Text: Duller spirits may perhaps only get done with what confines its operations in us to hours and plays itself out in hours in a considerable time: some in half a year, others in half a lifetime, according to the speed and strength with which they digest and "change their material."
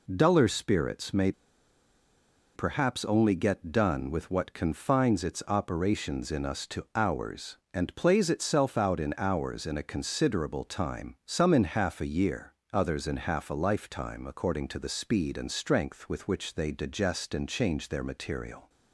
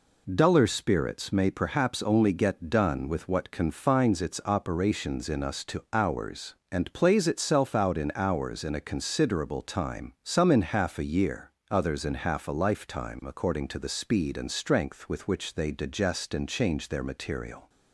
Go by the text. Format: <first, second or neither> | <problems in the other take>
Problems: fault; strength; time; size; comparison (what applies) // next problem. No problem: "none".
second | pauses between "may" and "perhaps"; at 1.3 s; 1.2 s long